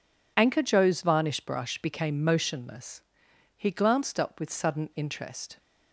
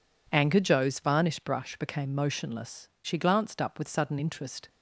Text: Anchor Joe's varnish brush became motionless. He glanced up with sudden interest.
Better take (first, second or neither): first